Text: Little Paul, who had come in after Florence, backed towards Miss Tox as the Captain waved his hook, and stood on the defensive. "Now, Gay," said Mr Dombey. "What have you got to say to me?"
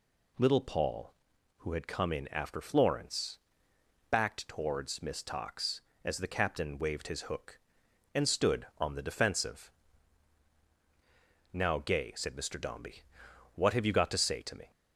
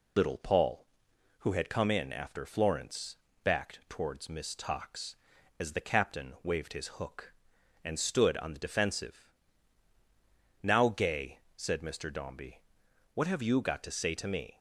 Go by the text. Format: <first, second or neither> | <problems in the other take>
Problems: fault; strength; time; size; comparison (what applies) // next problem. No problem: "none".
first | loses the start of "Little"; at 0.1 s; 90 ms